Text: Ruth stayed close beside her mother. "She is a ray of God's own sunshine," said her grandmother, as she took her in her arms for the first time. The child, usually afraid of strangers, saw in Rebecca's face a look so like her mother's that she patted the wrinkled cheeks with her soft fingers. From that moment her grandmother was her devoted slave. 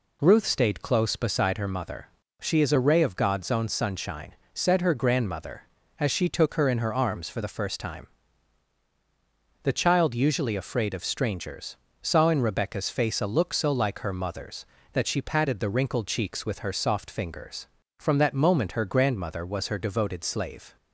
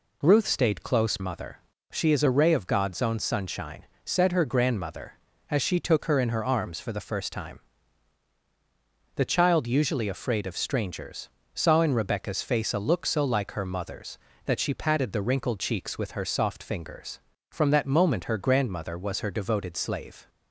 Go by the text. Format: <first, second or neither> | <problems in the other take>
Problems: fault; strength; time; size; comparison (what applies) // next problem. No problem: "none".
first | skips "beside her"; at 1.1 s